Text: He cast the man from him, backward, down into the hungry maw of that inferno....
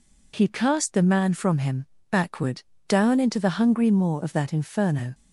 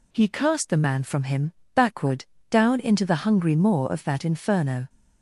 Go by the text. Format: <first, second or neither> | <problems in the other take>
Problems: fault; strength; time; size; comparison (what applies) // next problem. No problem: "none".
neither | none